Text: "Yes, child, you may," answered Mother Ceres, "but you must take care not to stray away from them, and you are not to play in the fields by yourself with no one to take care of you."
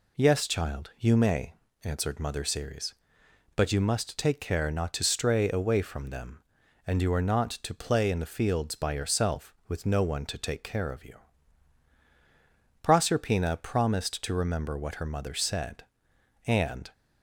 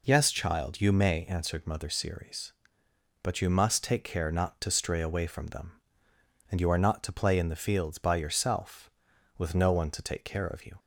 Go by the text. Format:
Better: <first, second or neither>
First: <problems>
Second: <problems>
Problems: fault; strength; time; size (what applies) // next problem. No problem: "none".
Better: second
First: goes on to say "Proserpina promised to remember what her mother said and"; strong; from 12.8 s on; 4.1 s long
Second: none